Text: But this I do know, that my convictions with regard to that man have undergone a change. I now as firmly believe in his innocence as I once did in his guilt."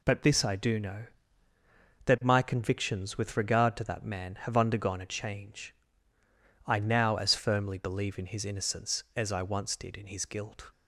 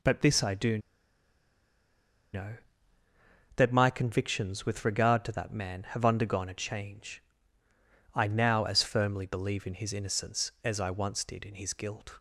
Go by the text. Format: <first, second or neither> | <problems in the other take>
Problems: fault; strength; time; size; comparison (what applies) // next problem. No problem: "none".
first | pauses between "do" and "know"; strong; at 0.7 s; 1.5 s long